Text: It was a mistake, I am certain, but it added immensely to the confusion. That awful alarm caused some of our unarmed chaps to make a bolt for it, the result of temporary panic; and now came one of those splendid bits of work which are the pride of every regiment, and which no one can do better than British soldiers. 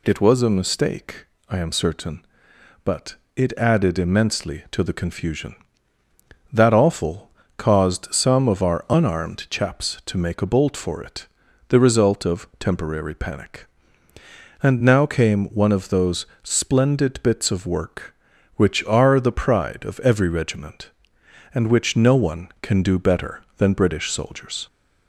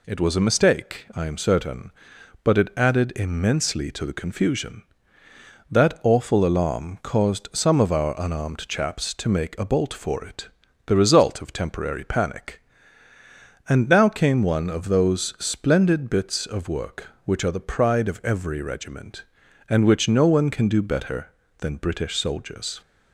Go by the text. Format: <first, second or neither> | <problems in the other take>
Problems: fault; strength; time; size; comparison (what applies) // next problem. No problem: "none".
second | pauses between "but" and "it"; slight; at 3.1 s; 0.22 s long // skips "alarm"; at 7.4 s // pauses between "those" and "splendid"; slight; at 16.2 s; 0.16 s long